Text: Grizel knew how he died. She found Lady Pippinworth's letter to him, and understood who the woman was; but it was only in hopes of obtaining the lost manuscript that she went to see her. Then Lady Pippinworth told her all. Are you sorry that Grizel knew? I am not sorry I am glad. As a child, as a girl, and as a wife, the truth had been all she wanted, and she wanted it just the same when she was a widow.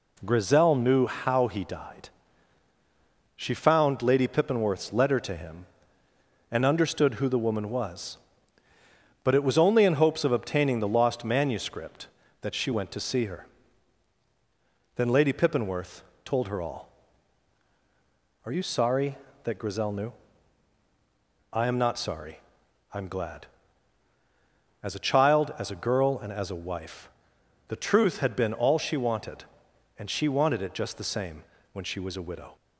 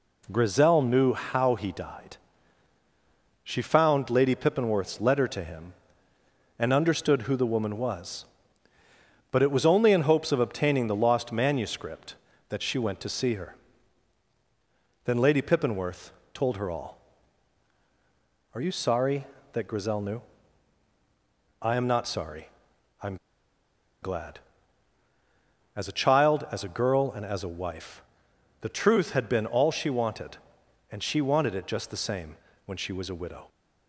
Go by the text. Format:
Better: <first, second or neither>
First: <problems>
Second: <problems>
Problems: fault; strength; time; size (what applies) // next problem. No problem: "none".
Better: first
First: pauses between "Pippinworth" and "told"; slight; at 16.0 s; 0.22 s long // pauses between "sorry" and "I"; noticeable; at 22.3 s; 0.54 s long // pauses between "same" and "when"; slight; at 31.4 s; 0.32 s long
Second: pauses between "Pippinworth" and "told"; slight; at 16.1 s; 0.22 s long // pauses between "sorry" and "I"; noticeable; at 22.4 s; 0.54 s long // pauses between "am" and "glad"; noticeable; at 23.1 s; 0.85 s long // pauses between "same" and "when"; slight; at 32.3 s; 0.32 s long